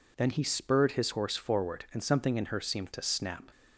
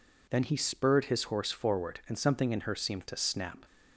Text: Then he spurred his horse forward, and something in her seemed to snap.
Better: neither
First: none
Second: none

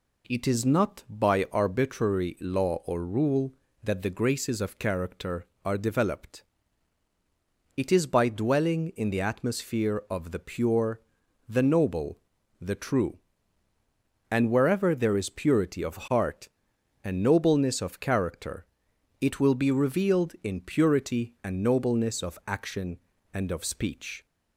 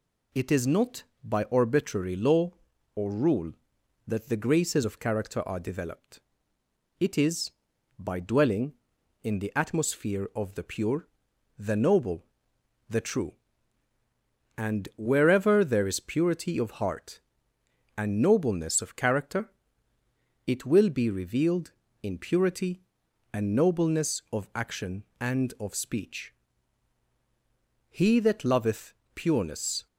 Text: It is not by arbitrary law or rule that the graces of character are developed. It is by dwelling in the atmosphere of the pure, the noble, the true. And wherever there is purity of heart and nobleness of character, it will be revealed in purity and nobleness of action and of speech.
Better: first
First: none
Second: goes on to say "He that loveth pureness"; strong; from 27.8 s on; 1.9 s long

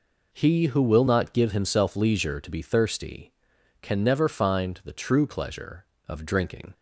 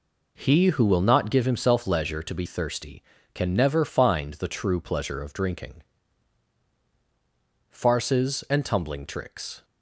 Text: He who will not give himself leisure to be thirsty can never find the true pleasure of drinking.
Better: first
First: none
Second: goes on to say "Farces and tumbling tricks"; strong; from 7.7 s on; 1.9 s long

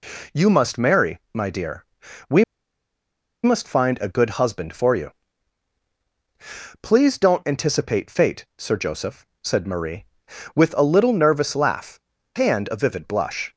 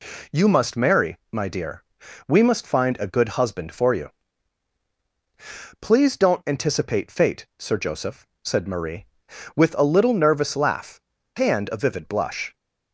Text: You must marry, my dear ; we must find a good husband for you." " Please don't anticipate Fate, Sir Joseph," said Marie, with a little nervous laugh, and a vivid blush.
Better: second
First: pauses between "we" and "must"; at 2.4 s; 0.99 s long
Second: none

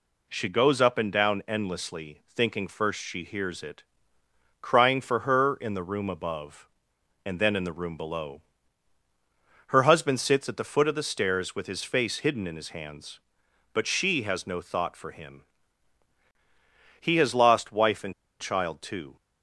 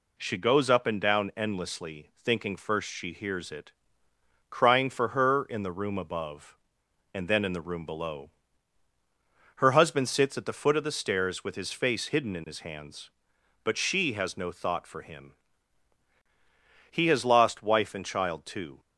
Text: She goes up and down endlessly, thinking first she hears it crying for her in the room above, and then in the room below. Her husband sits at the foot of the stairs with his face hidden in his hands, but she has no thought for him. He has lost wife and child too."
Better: second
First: pauses between "it" and "crying"; noticeable; at 3.8 s; 0.78 s long // pauses between "and" and "child"; slight; at 18.1 s; 0.27 s long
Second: pauses between "it" and "crying"; noticeable; at 3.7 s; 0.78 s long

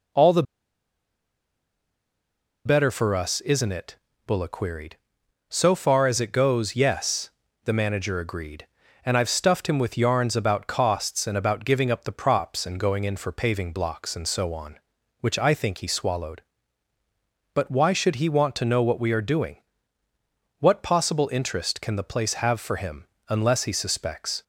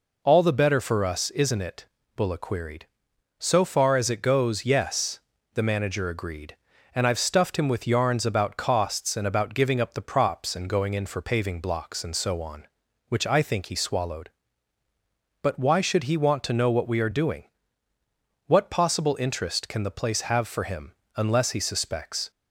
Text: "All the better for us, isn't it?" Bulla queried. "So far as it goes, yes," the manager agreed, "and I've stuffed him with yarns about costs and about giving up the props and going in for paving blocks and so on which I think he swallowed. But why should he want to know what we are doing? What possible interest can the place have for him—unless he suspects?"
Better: second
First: pauses between "the" and "better"; strong; at 0.4 s; 2.2 s long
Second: none

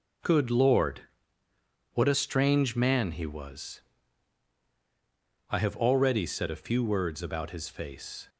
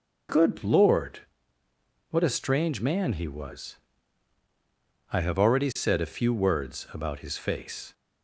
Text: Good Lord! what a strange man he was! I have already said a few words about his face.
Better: neither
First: none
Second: none

